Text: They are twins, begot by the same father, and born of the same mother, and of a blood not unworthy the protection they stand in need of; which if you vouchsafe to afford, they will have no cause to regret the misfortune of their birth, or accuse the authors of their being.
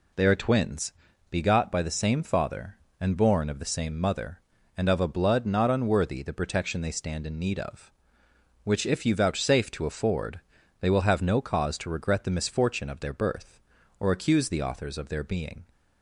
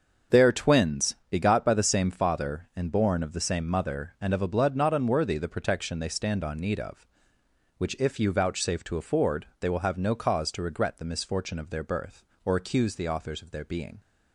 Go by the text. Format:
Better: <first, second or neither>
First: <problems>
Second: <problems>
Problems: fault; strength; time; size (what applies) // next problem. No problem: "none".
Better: first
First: none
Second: starts louder than the rest; until 1.4 s; 6.5 dB // says "on" for "in"; at 6.4 s